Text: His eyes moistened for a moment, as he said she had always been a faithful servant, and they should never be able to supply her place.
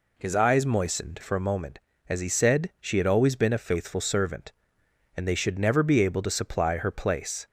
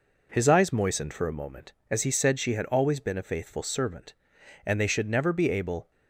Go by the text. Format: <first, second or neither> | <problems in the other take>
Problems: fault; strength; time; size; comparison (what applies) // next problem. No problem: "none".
first | stops before "to supply her place"; at 5.9 s